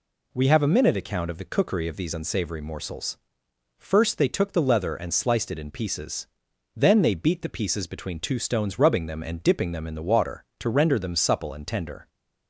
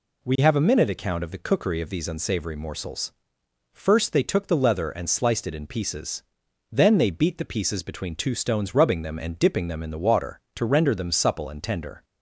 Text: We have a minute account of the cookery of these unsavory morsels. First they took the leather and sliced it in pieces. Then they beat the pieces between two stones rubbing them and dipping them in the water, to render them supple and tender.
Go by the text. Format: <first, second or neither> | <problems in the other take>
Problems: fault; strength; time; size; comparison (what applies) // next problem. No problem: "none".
neither | none